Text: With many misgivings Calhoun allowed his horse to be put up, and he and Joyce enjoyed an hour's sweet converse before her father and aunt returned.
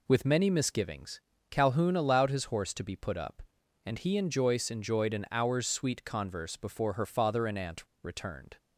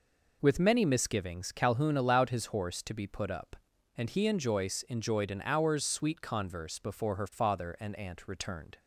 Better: second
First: pauses between "misgivings" and "Calhoun"; slight; at 1.2 s; 0.30 s long // pauses between "aunt" and "returned"; slight; at 7.8 s; 0.21 s long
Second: none

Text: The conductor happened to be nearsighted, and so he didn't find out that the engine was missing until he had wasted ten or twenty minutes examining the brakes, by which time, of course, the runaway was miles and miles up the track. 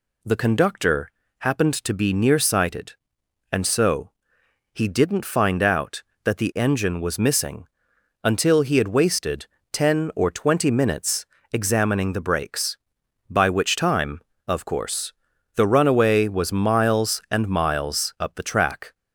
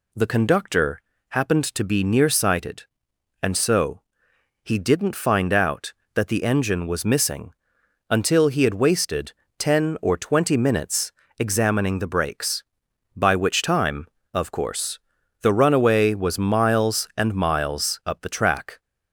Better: neither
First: pauses between "conductor" and "happened"; slight; at 1.0 s; 0.30 s long // pauses between "so" and "he"; noticeable; at 4.1 s; 0.60 s long // pauses between "missing" and "until"; noticeable; at 7.6 s; 0.56 s long // pauses between "wasted" and "ten"; slight; at 9.4 s; 0.26 s long // pauses between "minutes" and "examining"; slight; at 11.2 s; 0.26 s long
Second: pauses between "conductor" and "happened"; slight; at 0.9 s; 0.30 s long // pauses between "so" and "he"; noticeable; at 4.0 s; 0.60 s long // pauses between "missing" and "until"; noticeable; at 7.5 s; 0.56 s long // pauses between "wasted" and "ten"; slight; at 9.3 s; 0.26 s long // pauses between "minutes" and "examining"; slight; at 11.1 s; 0.26 s long

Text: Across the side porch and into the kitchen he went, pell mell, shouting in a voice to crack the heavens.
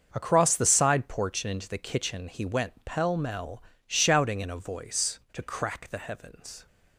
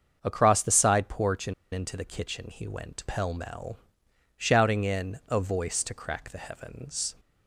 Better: first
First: starts louder than the rest; until 1.1 s; 7 dB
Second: starts louder than the rest; until 1.2 s; 7 dB // pauses between "and" and "into"; slight; at 1.5 s; 0.19 s long

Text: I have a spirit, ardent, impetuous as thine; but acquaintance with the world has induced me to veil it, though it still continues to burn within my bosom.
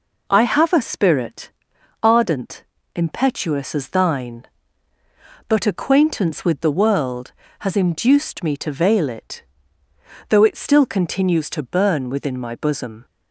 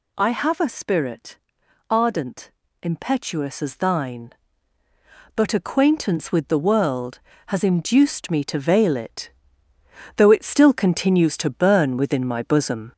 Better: first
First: none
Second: gets louder; noticeable; throughout; 4.5 dB

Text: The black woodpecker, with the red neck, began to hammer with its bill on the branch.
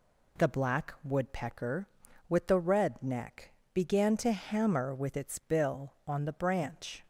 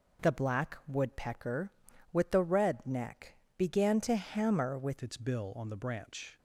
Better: first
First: none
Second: changes voice at "its"; from 5.0 s on; 1.3 s long

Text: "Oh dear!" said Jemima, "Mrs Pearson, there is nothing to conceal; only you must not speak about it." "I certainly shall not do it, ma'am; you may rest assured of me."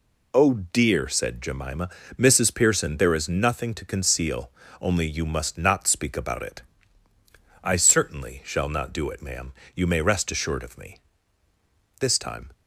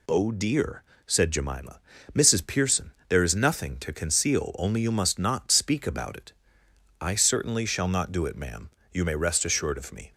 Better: second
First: goes on to say "This time"; from 11.9 s on; 0.52 s long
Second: none

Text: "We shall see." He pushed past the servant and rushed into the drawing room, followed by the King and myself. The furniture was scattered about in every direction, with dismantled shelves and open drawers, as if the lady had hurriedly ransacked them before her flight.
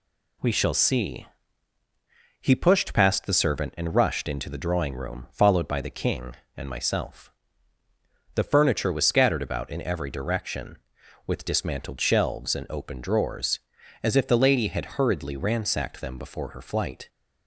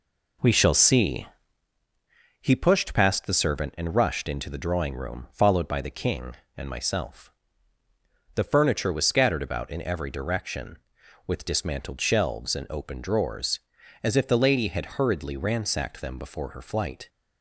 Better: first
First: none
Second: starts louder than the rest; until 1.6 s; 4 dB

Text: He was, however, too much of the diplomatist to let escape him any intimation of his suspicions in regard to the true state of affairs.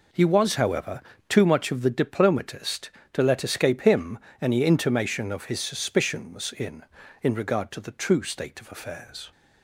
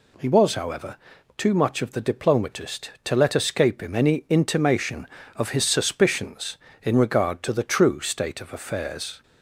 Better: second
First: pauses between "him" and "any"; slight; at 4.1 s; 0.22 s long // says "in" twice; at 7.2 s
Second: none

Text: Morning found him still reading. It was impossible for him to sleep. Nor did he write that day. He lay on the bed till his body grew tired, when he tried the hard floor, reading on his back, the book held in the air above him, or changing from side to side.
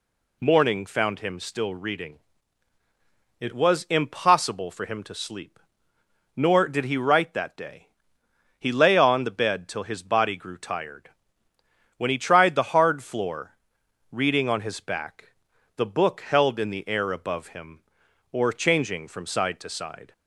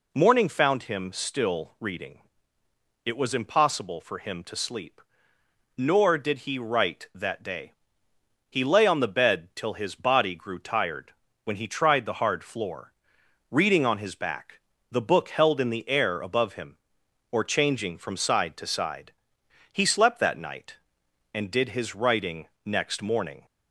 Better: first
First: none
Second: goes on to say "He slept that night and did his writing next morning"; strong; from 19.7 s on; 3.7 s long

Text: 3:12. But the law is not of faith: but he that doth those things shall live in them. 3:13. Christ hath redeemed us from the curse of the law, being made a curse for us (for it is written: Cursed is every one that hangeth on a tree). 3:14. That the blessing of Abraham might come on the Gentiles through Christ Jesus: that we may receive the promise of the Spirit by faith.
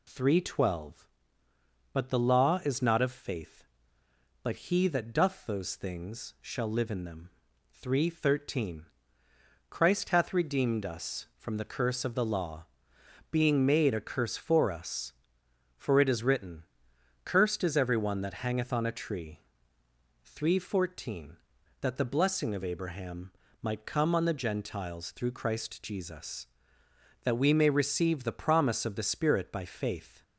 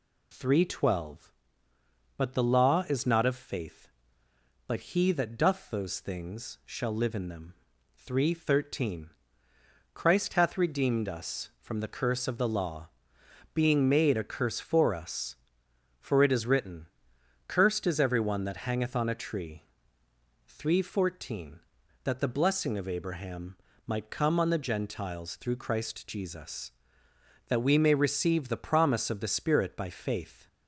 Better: neither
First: pauses between "Abraham" and "might"; slight; at 23.3 s; 0.28 s long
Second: pauses between "Abraham" and "might"; slight; at 23.5 s; 0.28 s long

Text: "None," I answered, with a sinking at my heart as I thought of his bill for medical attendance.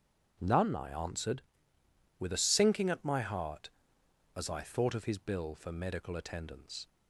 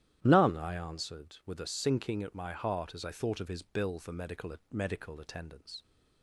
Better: first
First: starts louder than the rest; strong; until 1.4 s; 7.5 dB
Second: starts louder than the rest; strong; until 1.2 s; 12 dB // says "medical" twice; at 4.7 s

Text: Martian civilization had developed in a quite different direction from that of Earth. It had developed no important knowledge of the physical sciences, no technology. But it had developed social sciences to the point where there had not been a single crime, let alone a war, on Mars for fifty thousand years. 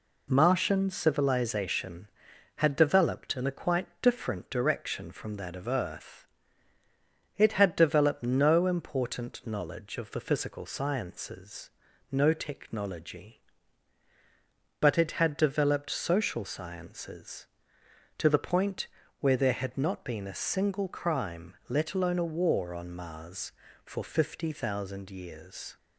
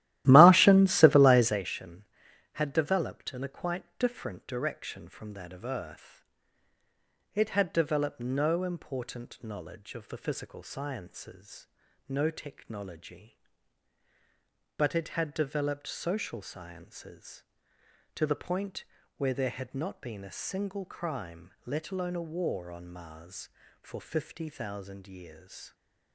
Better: first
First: pauses between "quite" and "different"; slight; at 3.8 s; 0.16 s long // pauses between "point" and "where"; slight; at 18.8 s; 0.34 s long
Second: starts louder than the rest; strong; until 1.7 s; 15 dB // pauses between "quite" and "different"; slight; at 3.8 s; 0.16 s long // pauses between "point" and "where"; slight; at 18.8 s; 0.34 s long

